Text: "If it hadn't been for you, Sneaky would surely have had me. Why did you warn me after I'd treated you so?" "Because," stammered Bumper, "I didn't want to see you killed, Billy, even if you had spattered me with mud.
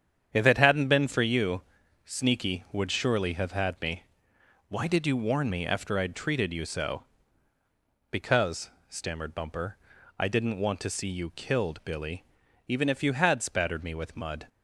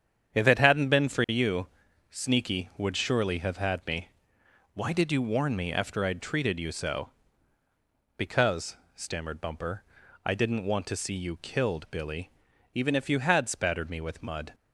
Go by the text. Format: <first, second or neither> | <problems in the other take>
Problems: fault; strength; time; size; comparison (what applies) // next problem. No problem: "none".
neither | starts louder than the rest; strong; the same in both